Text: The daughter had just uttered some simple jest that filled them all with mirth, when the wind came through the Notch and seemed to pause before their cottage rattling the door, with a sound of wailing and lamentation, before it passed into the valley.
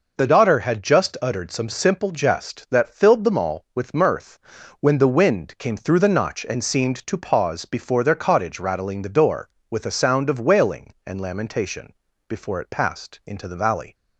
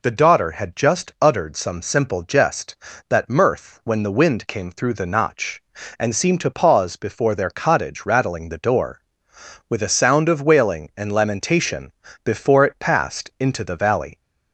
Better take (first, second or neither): first